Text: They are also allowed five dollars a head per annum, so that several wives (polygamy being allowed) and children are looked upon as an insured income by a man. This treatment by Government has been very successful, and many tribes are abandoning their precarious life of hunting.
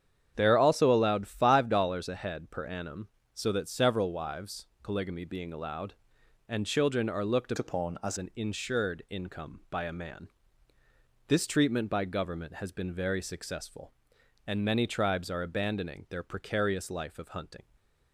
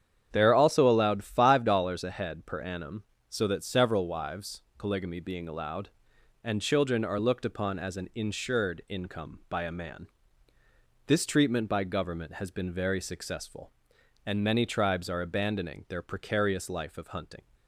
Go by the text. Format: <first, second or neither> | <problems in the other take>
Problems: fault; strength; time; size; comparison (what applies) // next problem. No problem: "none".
second | starts louder than the rest; strong; until 1.3 s; 8.5 dB; strong in the second // changes voice from "upon" to "as"; from 7.5 to 8.1 s; 0.6 s long